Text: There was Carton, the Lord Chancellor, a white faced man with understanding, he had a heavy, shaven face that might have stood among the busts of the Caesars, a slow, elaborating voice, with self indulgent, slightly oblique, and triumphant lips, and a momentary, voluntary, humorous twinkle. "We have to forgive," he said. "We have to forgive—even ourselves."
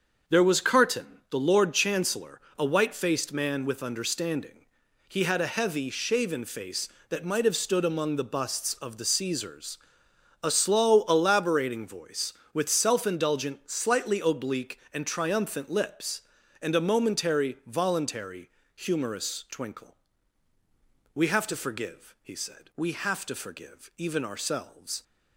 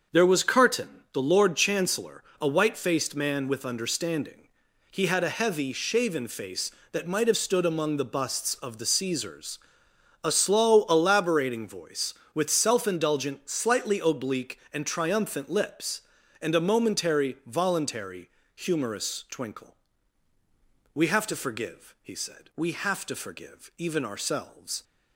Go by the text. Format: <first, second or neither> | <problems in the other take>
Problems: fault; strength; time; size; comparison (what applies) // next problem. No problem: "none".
neither | starts louder than the rest; the same in both